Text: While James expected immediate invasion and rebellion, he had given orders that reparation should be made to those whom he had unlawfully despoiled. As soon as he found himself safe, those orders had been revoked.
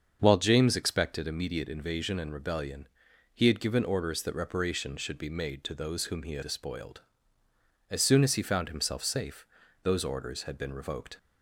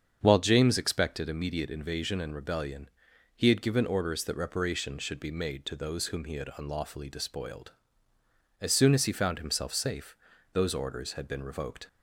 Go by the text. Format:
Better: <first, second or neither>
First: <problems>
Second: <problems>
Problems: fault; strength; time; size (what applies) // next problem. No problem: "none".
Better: second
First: starts louder than the rest; until 1.2 s; 6.5 dB // skips "unlawfully"; at 6.4 s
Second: starts louder than the rest; strong; until 1.2 s; 7 dB